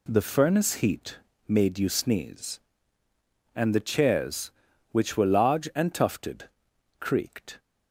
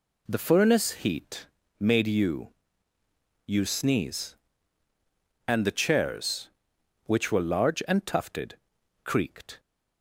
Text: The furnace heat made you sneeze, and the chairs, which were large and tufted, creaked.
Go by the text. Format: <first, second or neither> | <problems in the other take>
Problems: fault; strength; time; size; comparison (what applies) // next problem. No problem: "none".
first | pauses between "heat" and "made"; slight; at 1.4 s; 0.34 s long; slight in the first // says "you" twice; at 3.4 s